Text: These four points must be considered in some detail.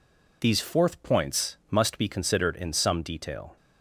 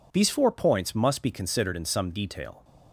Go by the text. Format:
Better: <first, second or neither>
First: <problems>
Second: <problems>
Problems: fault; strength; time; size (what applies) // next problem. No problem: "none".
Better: second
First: says "fourth" for "four"; at 0.5 s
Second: none